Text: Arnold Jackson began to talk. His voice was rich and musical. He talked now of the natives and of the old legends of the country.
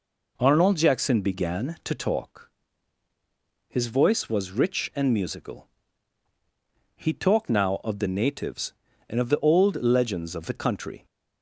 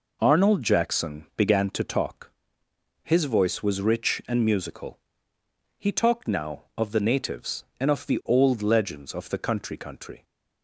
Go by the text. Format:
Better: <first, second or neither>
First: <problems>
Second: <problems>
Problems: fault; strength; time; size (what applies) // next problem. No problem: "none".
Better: first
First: none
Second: says "country" twice; at 9.7 s